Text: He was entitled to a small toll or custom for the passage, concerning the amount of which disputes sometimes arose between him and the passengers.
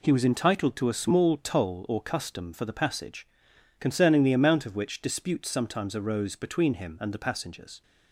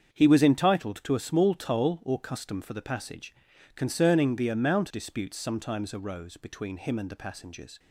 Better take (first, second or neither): first